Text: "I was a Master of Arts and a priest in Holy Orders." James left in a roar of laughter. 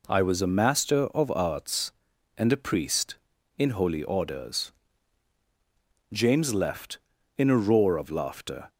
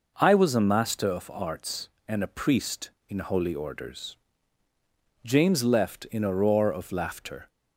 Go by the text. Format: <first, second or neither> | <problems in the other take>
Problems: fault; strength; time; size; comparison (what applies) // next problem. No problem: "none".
neither | none